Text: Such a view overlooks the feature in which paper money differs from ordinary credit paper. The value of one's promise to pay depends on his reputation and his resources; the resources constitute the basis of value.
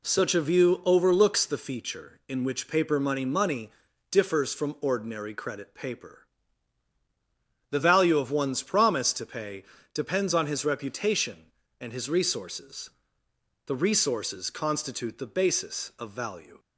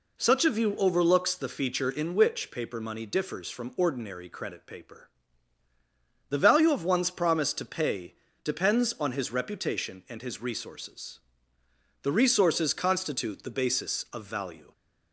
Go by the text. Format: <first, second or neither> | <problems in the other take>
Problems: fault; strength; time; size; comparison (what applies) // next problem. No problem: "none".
second | says "money" twice; at 3.2 s // pauses between "pay" and "depends"; slight; at 9.6 s; 0.30 s long; slight in the second